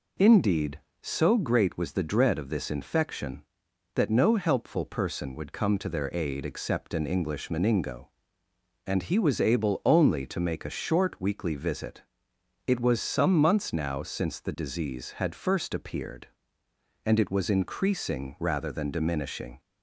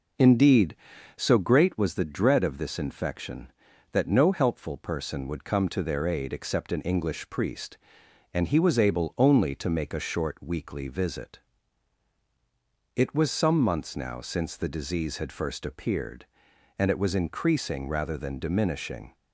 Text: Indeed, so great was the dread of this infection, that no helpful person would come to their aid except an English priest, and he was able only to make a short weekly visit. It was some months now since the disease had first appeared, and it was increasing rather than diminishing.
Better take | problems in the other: second | says "meningo" for "priest"; at 7.4 s

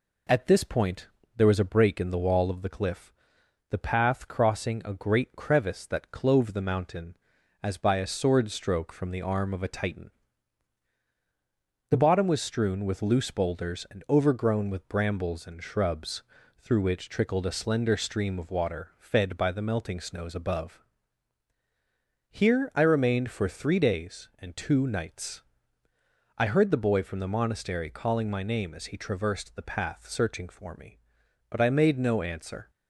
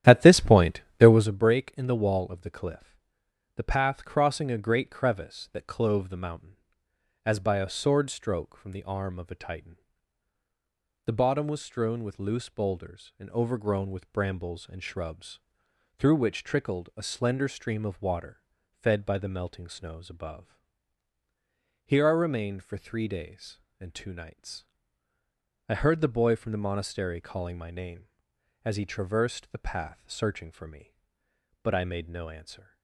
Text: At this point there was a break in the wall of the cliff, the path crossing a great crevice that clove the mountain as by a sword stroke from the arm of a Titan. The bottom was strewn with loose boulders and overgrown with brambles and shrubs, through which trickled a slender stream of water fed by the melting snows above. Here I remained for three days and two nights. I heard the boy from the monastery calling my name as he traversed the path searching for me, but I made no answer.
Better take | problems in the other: first | starts louder than the rest; strong; until 1.3 s; 12 dB // pauses between "point" and "there"; slight; at 0.8 s; 0.18 s long; slight in the first // pauses between "water" and "fed"; slight; at 18.4 s; 0.34 s long

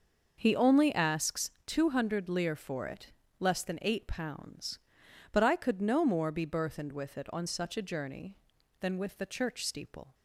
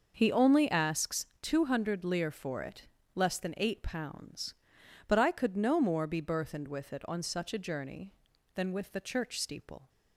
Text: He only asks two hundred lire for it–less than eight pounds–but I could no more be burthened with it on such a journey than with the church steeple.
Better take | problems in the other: neither | starts louder than the rest; noticeable; the same in both // pauses between "asks" and "two"; slight; the same in both

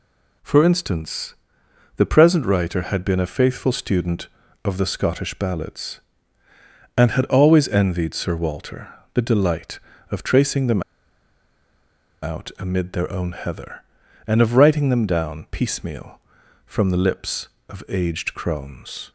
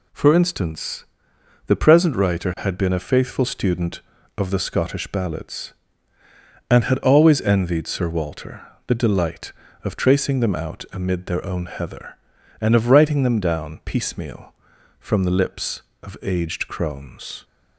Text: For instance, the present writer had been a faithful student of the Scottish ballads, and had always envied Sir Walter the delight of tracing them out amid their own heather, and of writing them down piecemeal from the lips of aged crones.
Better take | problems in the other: second | pauses between "Walter" and "the"; slight; at 8.8 s; 0.26 s long; slight in the second // pauses between "them" and "out"; strong; at 10.8 s; 1.4 s long

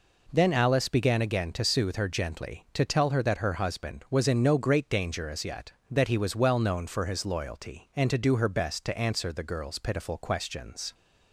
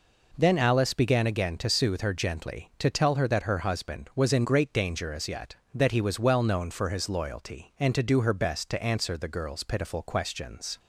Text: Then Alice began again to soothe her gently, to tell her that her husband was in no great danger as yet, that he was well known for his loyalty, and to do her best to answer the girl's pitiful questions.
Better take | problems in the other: first | skips "no"; at 4.4 s

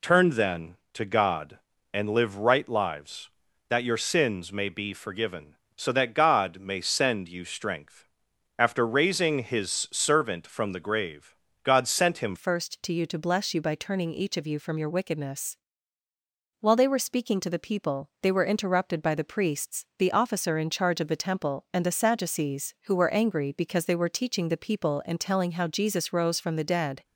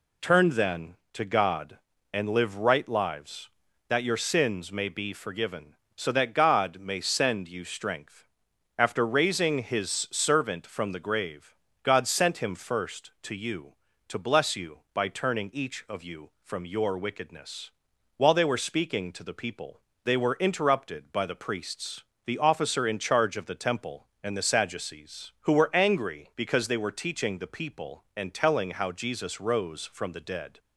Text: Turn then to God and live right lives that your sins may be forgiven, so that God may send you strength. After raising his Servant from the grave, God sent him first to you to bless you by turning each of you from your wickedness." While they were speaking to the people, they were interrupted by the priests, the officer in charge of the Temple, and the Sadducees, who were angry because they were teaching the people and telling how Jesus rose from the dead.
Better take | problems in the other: second | changes voice at "first"; from 12.3 s on; 14.7 s long

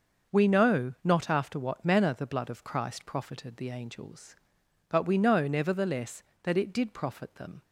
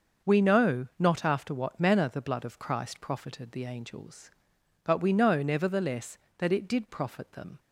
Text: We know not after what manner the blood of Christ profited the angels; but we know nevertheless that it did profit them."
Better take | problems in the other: neither | starts louder than the rest; the same in both

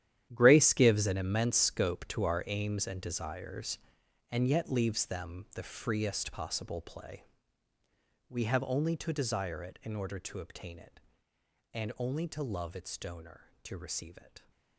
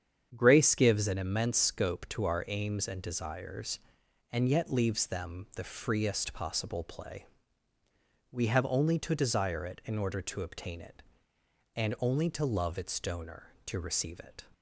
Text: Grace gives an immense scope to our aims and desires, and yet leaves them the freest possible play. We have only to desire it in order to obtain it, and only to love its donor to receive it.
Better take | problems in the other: second | gets quieter; strong; throughout; 14 dB // starts louder than the rest; strong; until 1.3 s; 11 dB; strong in the second

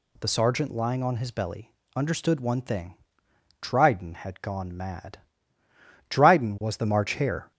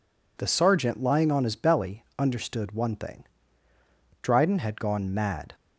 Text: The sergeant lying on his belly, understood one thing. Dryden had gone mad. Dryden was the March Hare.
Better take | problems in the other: first | stops before "Dryden was the March Hare"; at 5.5 s

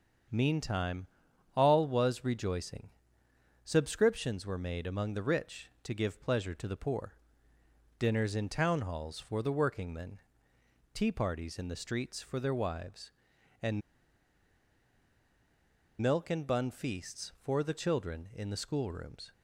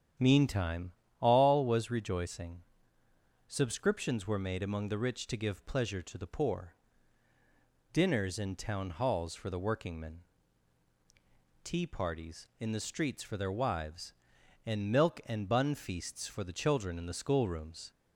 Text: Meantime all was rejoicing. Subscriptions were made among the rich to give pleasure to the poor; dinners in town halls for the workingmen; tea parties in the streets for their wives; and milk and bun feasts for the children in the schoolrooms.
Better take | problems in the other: second | starts louder than the rest; strong; until 1.8 s; 7.5 dB; strong in the second // pauses between "Meantime" and "all"; noticeable; at 1.0 s; 0.50 s long; slight in the second // pauses between "and" and "milk"; strong; at 13.8 s; 2.2 s long

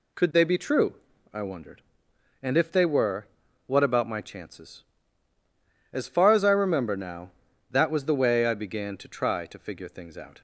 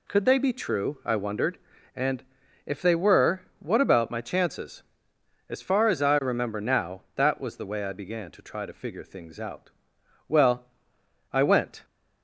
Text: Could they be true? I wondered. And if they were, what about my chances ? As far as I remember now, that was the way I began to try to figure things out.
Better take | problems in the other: first | pauses between "And" and "if"; at 2.2 s; 0.42 s long // goes on to say "Well I went"; from 10.2 s on; 1.5 s long

